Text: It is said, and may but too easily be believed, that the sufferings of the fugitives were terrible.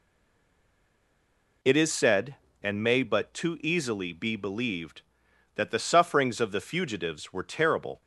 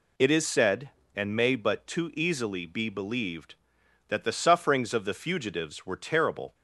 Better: second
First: stays silent before the first word; noticeable; until 1.6 s; 1.6 s long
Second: none

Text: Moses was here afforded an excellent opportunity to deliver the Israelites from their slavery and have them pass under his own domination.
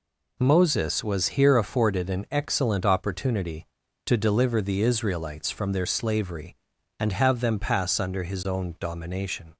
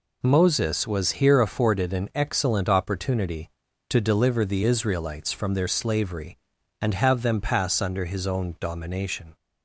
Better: neither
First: none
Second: none

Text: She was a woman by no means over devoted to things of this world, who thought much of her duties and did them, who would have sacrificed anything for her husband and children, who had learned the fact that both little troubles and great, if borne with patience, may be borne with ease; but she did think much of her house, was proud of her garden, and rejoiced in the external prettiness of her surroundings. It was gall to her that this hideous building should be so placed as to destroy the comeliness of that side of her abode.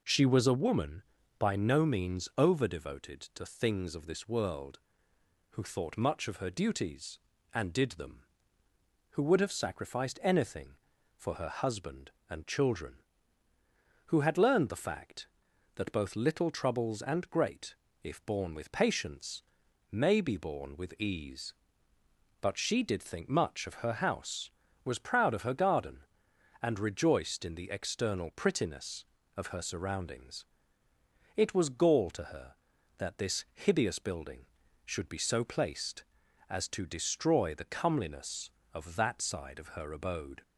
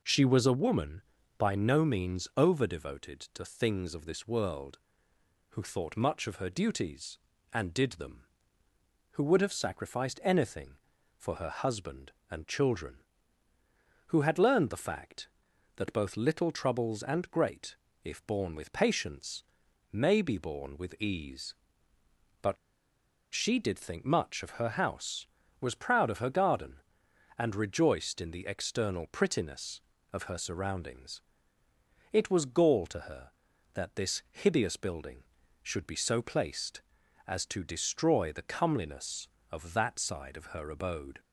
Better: first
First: none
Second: pauses between "but" and "she"; noticeable; at 22.5 s; 0.78 s long

